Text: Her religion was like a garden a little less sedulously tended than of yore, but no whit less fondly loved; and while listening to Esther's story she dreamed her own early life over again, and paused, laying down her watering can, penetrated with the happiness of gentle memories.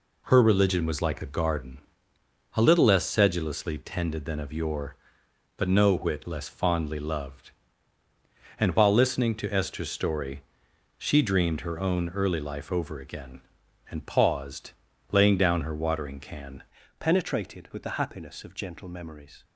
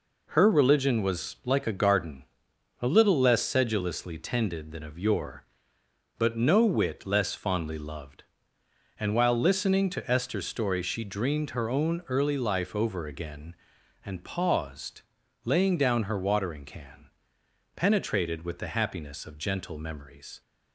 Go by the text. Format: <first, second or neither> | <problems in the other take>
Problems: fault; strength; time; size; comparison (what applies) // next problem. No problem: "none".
second | pauses between "garden" and "a"; noticeable; at 1.7 s; 0.76 s long; noticeable in the second // pauses between "story" and "she"; noticeable; at 10.4 s; 0.54 s long // changes voice at "penetrated"; from 16.9 s on; 2.5 s long